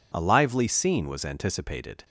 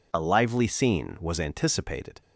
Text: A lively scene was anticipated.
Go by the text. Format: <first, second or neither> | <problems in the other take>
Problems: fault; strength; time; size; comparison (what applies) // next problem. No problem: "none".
neither | none